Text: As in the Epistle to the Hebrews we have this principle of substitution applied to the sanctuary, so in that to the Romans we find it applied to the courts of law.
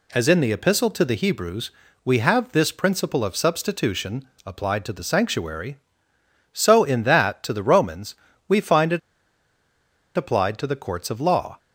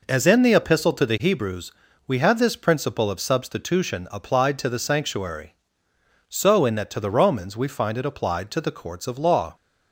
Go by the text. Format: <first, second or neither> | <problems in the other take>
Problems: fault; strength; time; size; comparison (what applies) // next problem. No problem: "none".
second | pauses between "Hebrews" and "we"; slight; at 1.7 s; 0.32 s long; slight in the second // pauses between "substitution" and "applied"; slight; at 4.2 s; 0.20 s long // pauses between "Romans" and "we"; slight; at 8.1 s; 0.34 s long // pauses between "it" and "applied"; at 8.9 s; 1.1 s long